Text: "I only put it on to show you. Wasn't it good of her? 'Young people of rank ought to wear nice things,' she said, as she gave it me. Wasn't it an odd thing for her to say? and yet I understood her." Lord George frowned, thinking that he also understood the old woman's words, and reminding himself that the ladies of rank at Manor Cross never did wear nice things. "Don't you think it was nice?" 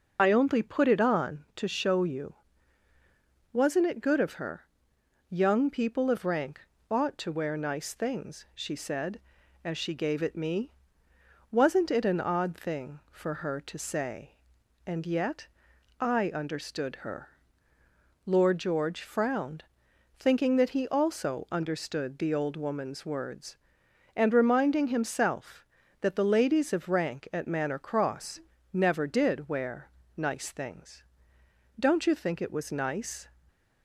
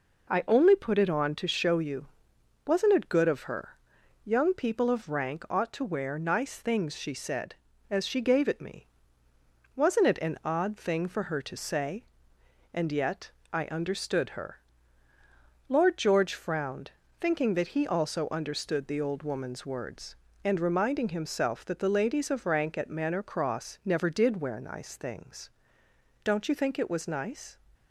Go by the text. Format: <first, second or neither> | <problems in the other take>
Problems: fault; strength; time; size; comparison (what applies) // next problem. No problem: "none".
second | loses the start of "I"; at 0.1 s; 35 ms // pauses between "rank" and "ought"; slight; at 6.6 s; 0.28 s long // pauses between "yet" and "I"; noticeable; at 15.4 s; 0.50 s long; slight in the second // pauses between "Cross" and "never"; slight; at 28.3 s; 0.34 s long // pauses between "wear" and "nice"; slight; at 29.8 s; 0.28 s long